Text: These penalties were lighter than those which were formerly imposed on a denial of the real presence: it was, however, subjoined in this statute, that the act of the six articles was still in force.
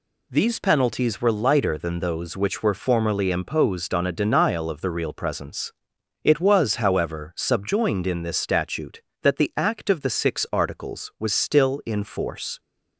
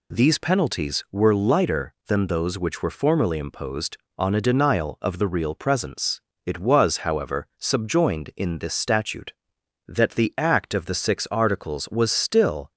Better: first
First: none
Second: stops before "in force"; at 12.7 s

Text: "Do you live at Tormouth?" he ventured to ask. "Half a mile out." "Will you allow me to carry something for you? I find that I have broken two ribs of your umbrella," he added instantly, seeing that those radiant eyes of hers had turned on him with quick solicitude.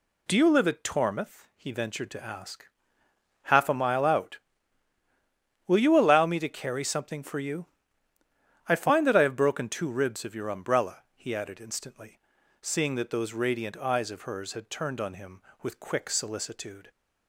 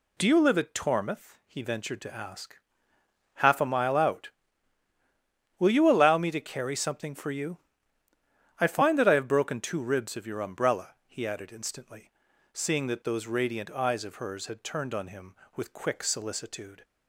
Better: neither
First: none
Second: none

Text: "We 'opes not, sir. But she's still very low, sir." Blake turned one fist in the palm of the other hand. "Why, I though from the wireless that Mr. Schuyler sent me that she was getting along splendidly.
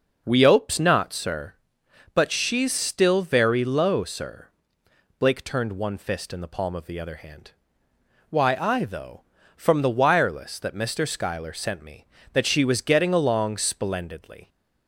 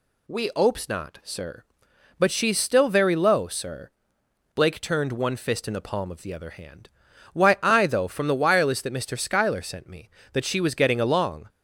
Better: first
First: none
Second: stops before "splendidly"; at 11.4 s

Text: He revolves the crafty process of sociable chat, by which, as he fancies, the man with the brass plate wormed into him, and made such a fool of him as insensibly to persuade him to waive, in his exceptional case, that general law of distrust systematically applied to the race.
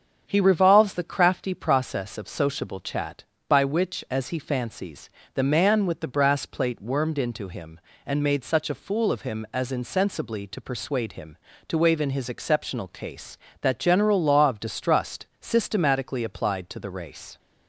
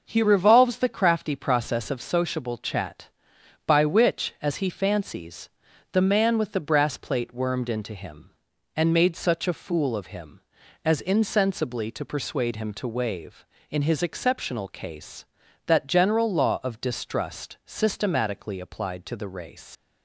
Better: first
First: starts louder than the rest; strong; until 1.2 s; 7.5 dB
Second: starts louder than the rest; noticeable; until 1.0 s; 6 dB // leaves "race" unfinished; at 19.7 s; 80 ms

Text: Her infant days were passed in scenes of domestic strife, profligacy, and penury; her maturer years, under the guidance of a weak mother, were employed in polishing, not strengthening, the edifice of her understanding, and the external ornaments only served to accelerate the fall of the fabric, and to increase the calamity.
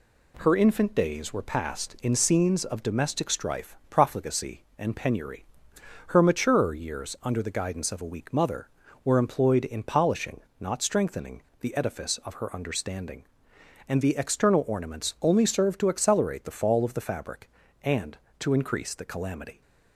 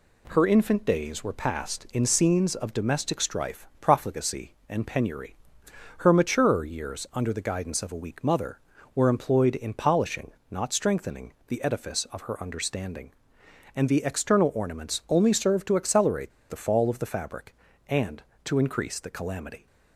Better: first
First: none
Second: pauses between "accelerate" and "the"; slight; at 16.3 s; 0.18 s long

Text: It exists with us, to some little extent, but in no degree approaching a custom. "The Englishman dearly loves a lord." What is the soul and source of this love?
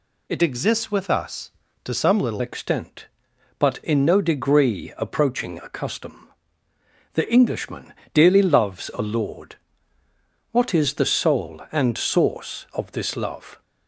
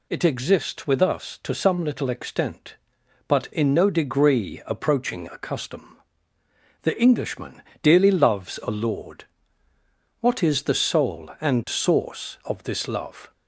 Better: second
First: changes voice from "exists" to "little"; from 0.4 to 2.4 s; 2.0 s long // pauses between "Englishman" and "dearly"; slight; at 7.9 s; 0.20 s long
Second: pauses between "Englishman" and "dearly"; slight; at 7.6 s; 0.20 s long

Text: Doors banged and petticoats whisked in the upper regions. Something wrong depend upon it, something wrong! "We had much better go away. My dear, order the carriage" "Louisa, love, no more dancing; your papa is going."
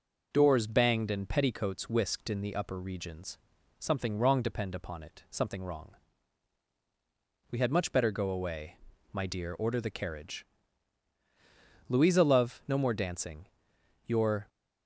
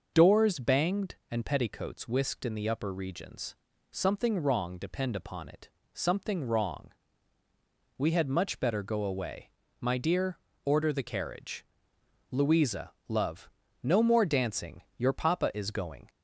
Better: second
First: pauses between "carriage" and "Louisa"; strong; at 10.4 s; 1.4 s long // stops before "papa is going"; at 14.4 s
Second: pauses between "carriage" and "Louisa"; noticeable; at 11.6 s; 0.64 s long

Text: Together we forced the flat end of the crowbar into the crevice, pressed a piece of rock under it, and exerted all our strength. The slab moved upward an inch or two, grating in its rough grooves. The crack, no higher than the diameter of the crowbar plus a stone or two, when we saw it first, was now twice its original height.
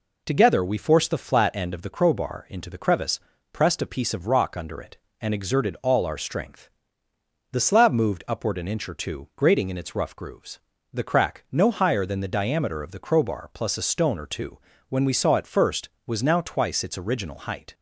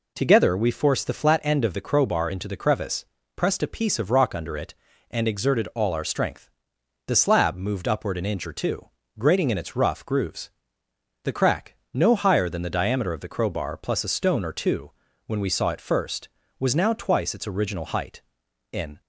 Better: first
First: none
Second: goes on to say "In"; slight; from 18.7 s on; 0.30 s long

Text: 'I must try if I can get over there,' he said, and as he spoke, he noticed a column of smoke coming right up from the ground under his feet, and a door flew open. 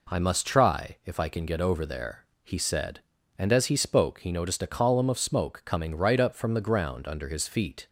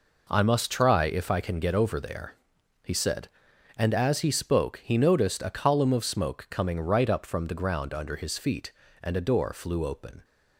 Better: second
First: stops before "and a door flew open"; at 7.8 s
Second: none

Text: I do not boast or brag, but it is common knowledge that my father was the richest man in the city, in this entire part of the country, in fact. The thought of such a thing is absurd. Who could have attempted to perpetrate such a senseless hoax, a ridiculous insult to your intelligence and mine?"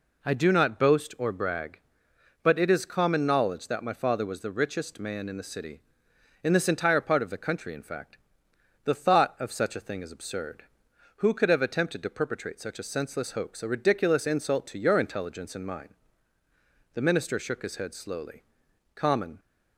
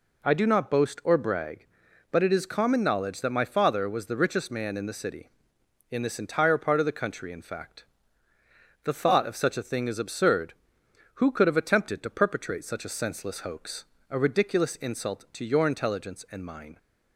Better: second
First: goes on to say "The minister shook his head slowly Common"; strong; from 16.9 s on; 2.4 s long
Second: none

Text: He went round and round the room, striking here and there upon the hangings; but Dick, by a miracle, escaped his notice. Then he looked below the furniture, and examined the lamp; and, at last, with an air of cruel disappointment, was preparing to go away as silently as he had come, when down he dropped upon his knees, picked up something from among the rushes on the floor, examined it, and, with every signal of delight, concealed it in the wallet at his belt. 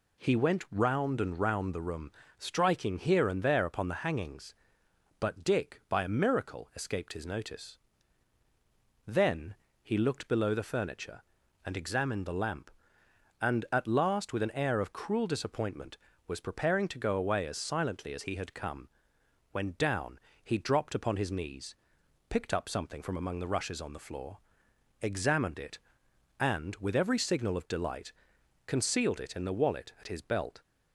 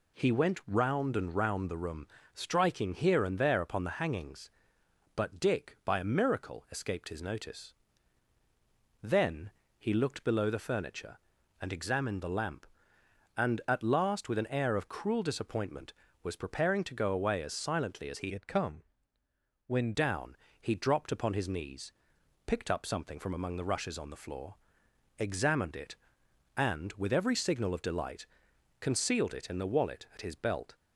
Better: first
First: pauses between "Then" and "he"; slight; at 9.5 s; 0.26 s long // pauses between "down" and "he"; slight; at 20.1 s; 0.24 s long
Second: pauses between "Then" and "he"; slight; at 9.5 s; 0.26 s long // changes voice from "had" to "when"; from 18.3 to 19.9 s; 1.6 s long // pauses between "down" and "he"; slight; at 20.3 s; 0.24 s long

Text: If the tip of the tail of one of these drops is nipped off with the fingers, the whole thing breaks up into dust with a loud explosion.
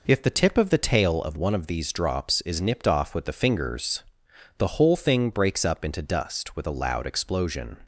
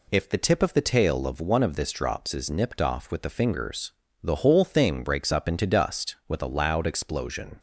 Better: first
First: none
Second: says "this" for "these"; at 1.7 s

